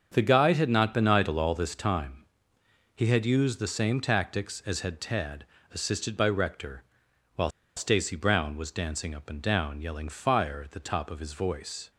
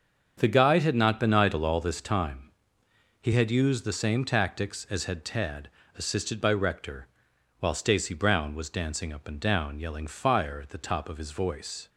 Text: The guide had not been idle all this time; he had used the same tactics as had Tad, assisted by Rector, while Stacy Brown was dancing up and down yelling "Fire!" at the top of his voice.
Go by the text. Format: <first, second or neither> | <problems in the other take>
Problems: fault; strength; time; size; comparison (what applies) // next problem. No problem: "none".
second | starts louder than the rest; until 1.1 s; 7 dB; also in the second // pauses between "while" and "Stacy"; slight; at 7.4 s; 0.28 s long